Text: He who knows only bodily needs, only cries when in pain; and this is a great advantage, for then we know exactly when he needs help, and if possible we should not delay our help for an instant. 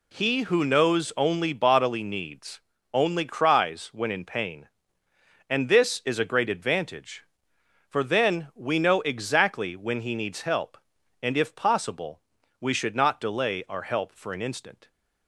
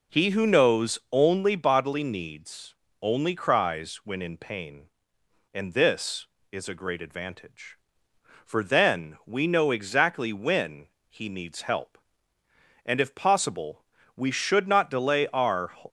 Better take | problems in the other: first | pauses between "when" and "he"; slight; at 10.8 s; 0.22 s long // pauses between "possible" and "we"; slight; at 13.8 s; 0.32 s long; also in the first // stops before "help for an instant"; at 15.8 s

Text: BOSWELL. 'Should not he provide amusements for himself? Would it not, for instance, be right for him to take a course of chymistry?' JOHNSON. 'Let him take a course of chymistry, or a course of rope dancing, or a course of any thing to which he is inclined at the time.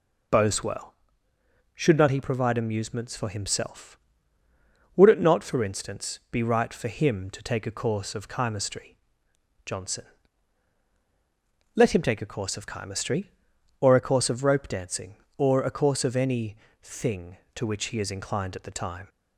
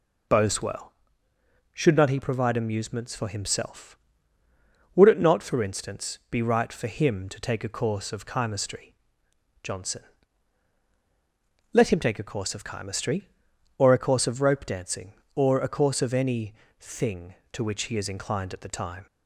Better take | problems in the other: neither | pauses between "any" and "thing"; slight; the same in both

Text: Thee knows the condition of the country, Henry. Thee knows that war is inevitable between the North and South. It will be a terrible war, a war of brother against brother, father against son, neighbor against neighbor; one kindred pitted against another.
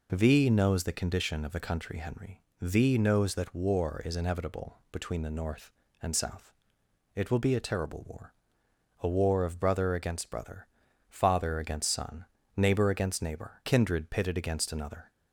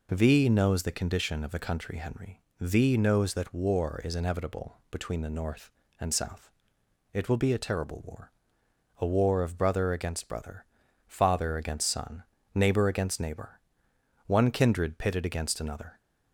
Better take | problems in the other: second | skips "one"; at 13.6 s

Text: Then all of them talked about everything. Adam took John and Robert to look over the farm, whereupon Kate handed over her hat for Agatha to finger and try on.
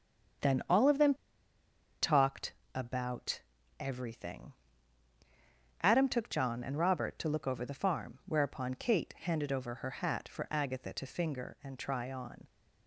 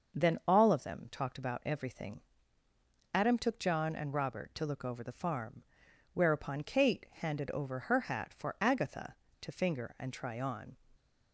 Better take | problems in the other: second | starts louder than the rest; strong; until 2.3 s; 7.5 dB; also in the second // pauses between "them" and "talked"; noticeable; at 1.1 s; 0.88 s long // pauses between "talked" and "about"; slight; at 2.5 s; 0.22 s long // pauses between "about" and "everything"; at 3.4 s; 0.38 s long

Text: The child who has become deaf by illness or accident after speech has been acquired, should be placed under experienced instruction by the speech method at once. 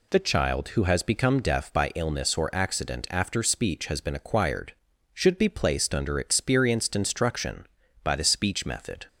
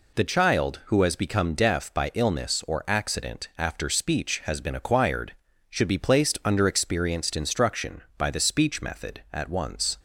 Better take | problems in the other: second | stops before "at once"; at 9.0 s

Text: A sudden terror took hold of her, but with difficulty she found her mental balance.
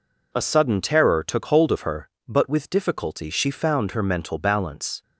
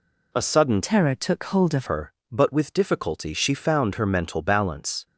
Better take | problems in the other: first | changes voice from "terror" to "of"; from 0.8 to 1.8 s; 1.0 s long

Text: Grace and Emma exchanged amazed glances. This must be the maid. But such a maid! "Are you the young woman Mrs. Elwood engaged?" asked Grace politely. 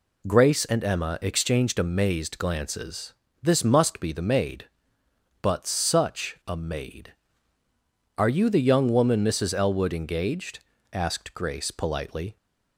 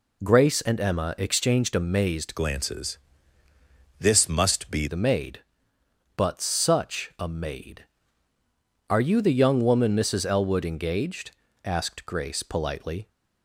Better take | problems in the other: first | changes voice from "glances" to "be"; from 2.3 to 4.8 s; 2.5 s long

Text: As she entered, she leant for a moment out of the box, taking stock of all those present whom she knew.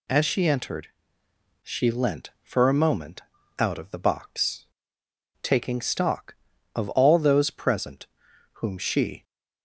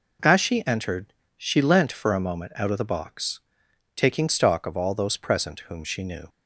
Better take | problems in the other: second | pauses between "moment" and "out"; slight; at 3.2 s; 0.36 s long // pauses between "present" and "whom"; noticeable; at 8.0 s; 0.48 s long // stops before "knew"; at 9.2 s

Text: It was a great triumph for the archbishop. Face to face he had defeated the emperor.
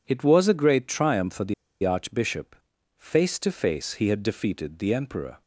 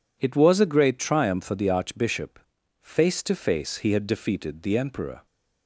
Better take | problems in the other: second | pauses between "the" and "archbishop"; slight; at 1.5 s; 0.29 s long

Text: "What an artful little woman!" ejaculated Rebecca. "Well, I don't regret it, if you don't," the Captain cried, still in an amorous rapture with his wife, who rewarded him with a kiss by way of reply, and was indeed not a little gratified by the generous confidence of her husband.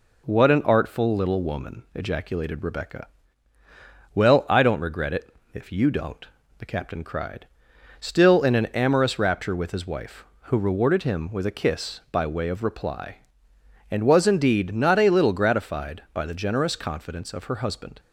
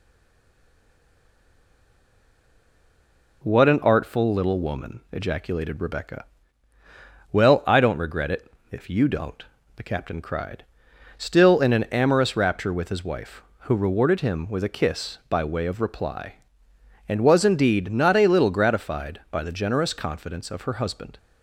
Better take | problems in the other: first | stays silent before the first word; strong; until 3.4 s; 3.4 s long

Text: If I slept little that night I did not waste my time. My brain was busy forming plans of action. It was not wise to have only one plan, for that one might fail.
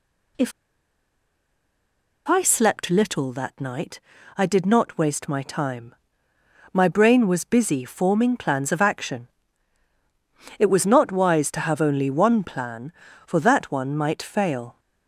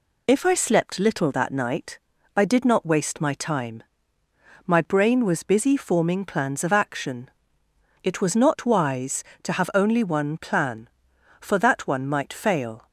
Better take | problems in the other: second | pauses between "If" and "I"; strong; at 0.5 s; 1.7 s long // pauses between "night" and "I"; slight; at 3.9 s; 0.36 s long; also in the second

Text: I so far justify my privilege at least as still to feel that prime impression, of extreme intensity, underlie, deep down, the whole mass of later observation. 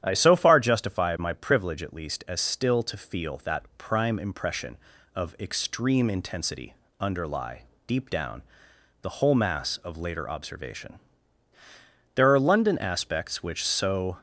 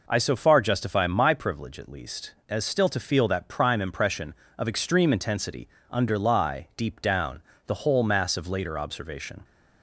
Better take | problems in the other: second | starts louder than the rest; strong; until 1.0 s; 10 dB // goes on to say "There are London aspects which so"; strong; from 12.1 s on; 2.0 s long

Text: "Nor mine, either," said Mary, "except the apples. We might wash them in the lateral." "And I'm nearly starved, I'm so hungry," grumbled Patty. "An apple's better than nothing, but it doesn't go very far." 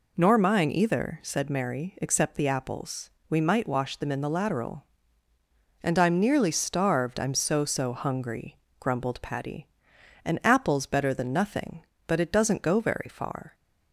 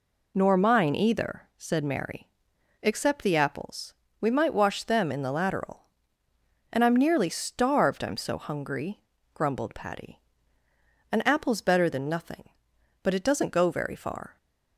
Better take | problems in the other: second | says "so" twice; at 7.6 s

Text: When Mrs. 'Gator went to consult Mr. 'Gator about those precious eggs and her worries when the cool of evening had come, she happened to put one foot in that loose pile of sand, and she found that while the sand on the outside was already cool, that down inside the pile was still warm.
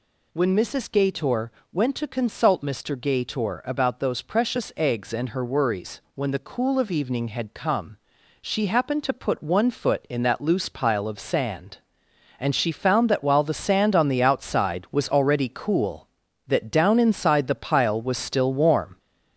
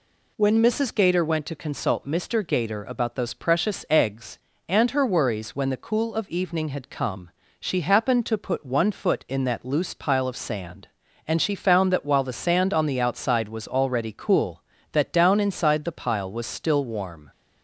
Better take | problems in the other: second | gets louder; noticeable; throughout; 4.5 dB // pauses between "Gator" and "went"; slight; at 1.5 s; 0.22 s long

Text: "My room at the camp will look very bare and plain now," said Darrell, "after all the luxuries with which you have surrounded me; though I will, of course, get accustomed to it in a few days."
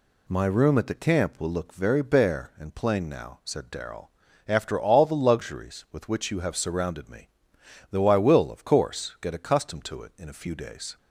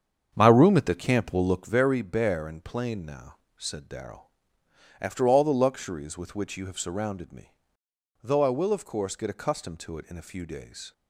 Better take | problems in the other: first | starts louder than the rest; strong; until 1.9 s; 7.5 dB

